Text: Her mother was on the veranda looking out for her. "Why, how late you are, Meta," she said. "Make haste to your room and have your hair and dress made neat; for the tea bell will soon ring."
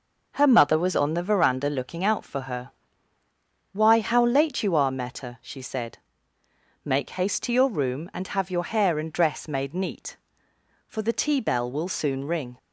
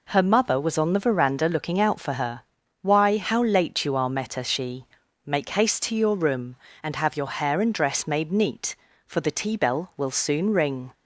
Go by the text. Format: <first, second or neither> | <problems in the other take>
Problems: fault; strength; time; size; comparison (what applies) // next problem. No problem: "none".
first | skips "said"; at 5.0 s